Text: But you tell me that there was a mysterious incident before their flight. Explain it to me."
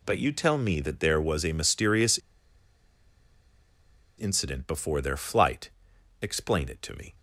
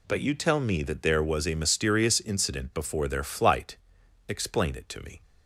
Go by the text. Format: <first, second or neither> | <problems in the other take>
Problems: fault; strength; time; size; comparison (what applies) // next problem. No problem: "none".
second | pauses between "mysterious" and "incident"; strong; at 2.1 s; 1.9 s long